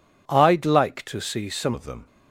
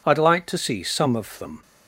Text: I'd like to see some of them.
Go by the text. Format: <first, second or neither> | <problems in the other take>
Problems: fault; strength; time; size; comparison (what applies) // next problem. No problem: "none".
second | changes voice at "of"; from 1.7 s on; 0.3 s long